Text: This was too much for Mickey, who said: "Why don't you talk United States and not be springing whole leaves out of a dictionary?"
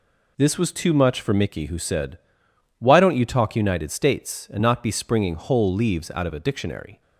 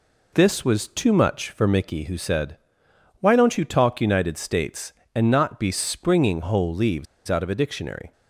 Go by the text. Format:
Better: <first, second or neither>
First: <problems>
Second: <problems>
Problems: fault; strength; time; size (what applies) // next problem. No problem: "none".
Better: first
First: none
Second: pauses between "leaves" and "out"; slight; at 7.0 s; 0.22 s long